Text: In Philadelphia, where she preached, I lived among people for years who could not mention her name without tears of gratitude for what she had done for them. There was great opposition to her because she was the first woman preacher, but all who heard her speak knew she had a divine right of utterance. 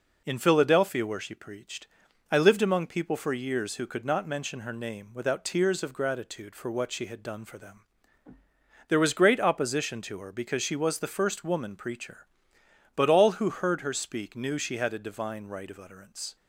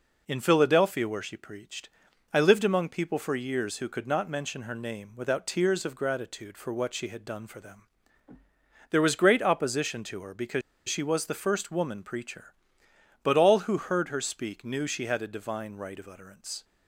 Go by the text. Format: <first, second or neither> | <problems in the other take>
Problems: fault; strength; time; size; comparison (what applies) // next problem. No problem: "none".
first | pauses between "because" and "she"; slight; at 10.6 s; 0.26 s long